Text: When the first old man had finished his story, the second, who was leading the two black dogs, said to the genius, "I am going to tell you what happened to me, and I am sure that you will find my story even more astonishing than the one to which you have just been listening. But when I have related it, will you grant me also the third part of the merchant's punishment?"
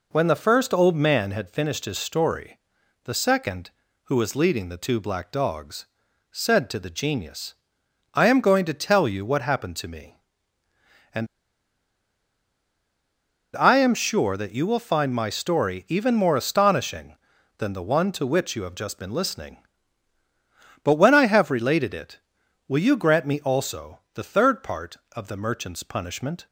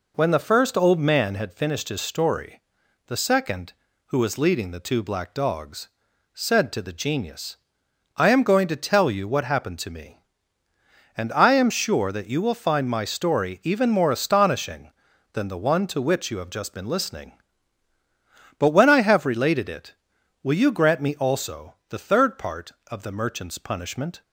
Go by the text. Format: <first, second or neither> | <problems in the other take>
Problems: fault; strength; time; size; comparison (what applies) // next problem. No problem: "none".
second | pauses between "and" and "I"; strong; at 11.2 s; 2.2 s long // pauses between "also" and "the"; slight; at 23.9 s; 0.16 s long; slight in the second